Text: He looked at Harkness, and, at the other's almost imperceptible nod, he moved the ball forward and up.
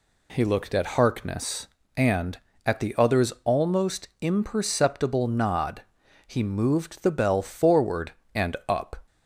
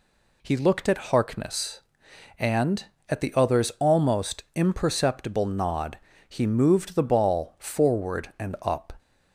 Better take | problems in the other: second | says "bell" for "ball"; at 7.1 s

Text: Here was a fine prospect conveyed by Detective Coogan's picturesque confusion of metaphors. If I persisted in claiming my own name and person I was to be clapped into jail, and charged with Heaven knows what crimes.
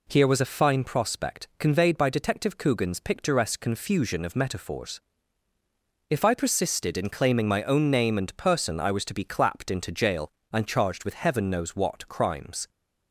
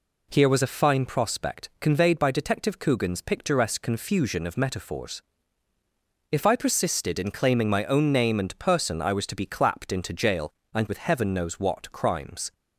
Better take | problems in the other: first | skips "charged"; at 10.8 s

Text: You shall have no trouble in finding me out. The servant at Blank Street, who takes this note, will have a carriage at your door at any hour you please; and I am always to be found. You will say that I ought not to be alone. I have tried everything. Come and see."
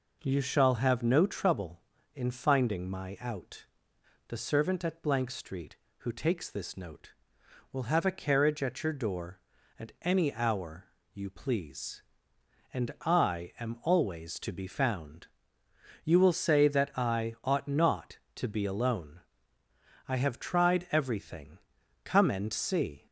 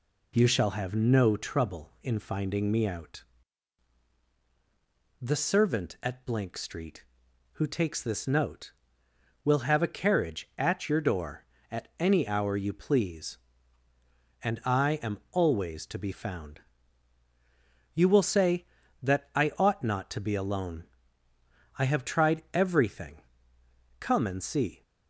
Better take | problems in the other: second | says "my" for "me"; at 2.9 s // pauses between "hour" and "you"; slight; at 10.8 s; 0.30 s long

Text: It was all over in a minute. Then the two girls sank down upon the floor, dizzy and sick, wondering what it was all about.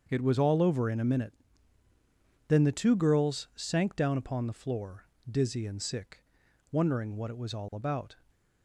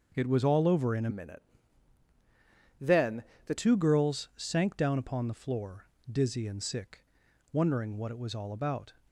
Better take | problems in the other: first | starts louder than the rest; until 1.1 s; 6.5 dB; also in the first // changes voice from "minute" to "the"; from 1.1 to 3.5 s; 2.4 s long // pauses between "Then" and "the"; slight; at 3.2 s; 0.24 s long

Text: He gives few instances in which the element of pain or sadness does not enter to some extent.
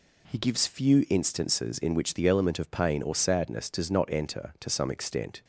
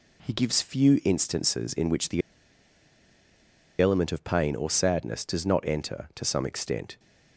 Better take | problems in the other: first | pauses between "the" and "element"; strong; at 2.2 s; 1.6 s long

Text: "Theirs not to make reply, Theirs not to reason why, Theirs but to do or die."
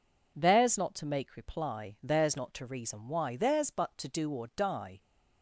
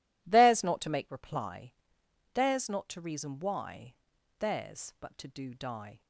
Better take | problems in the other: first | skips "or"; at 5.5 s

